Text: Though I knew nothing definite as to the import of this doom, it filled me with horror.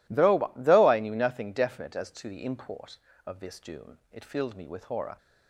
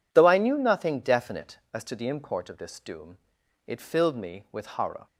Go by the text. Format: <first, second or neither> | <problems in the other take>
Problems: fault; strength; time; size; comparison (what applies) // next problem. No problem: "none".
second | says "Though" twice; at 0.5 s